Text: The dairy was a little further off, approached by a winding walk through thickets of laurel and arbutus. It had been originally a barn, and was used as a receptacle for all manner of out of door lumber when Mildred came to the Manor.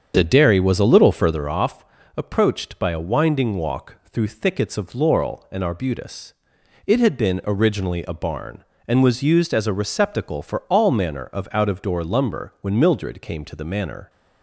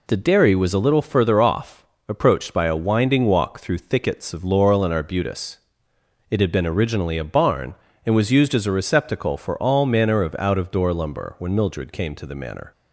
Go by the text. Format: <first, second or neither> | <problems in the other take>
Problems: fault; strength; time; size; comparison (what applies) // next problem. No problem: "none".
second | starts louder than the rest; strong; until 1.5 s; 7.5 dB